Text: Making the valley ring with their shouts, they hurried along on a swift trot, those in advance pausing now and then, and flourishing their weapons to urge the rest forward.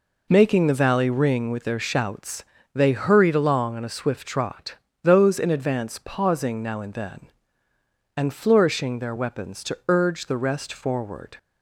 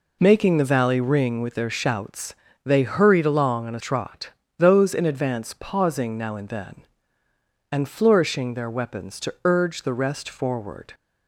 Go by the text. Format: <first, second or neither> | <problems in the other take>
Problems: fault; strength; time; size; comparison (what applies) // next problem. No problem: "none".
first | skips "swift"; at 3.8 s